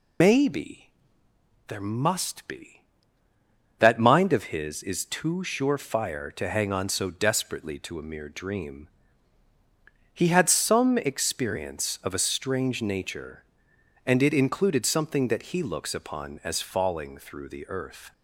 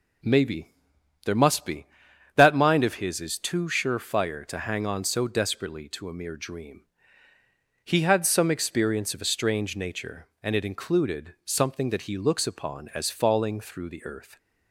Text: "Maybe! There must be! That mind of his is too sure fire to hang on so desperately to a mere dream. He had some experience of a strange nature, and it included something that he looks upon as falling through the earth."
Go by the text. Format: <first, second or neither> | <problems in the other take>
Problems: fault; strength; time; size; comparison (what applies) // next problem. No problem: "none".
second | loses the start of "Maybe"; at 0.2 s; 120 ms